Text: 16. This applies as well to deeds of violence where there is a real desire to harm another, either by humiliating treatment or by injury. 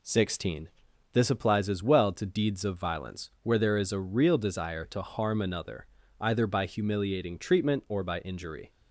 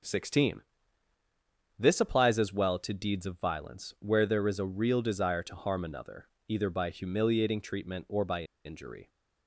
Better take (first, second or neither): first